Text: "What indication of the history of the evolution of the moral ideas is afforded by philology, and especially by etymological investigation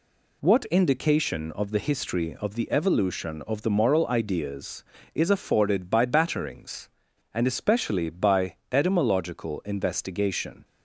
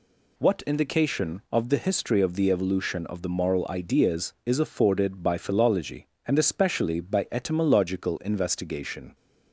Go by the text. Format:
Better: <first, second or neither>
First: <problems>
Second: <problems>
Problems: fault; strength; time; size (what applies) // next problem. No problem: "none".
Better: second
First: says "batterings" for "philology"; at 6.0 s // pauses between "by" and "etymological"; slight; at 8.5 s; 0.16 s long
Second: none